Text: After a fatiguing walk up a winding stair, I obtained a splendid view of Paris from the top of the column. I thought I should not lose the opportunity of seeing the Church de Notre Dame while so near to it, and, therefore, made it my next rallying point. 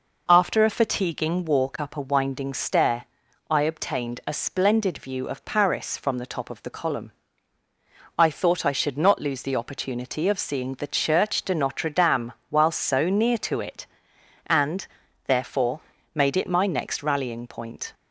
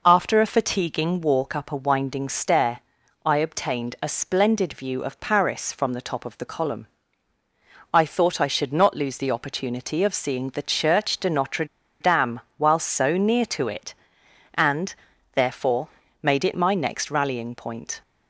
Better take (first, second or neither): first